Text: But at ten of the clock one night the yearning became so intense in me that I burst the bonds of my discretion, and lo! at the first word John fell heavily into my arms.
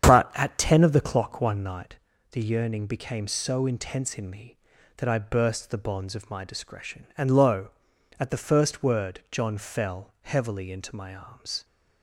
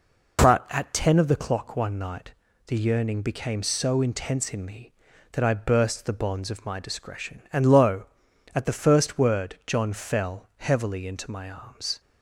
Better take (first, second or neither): second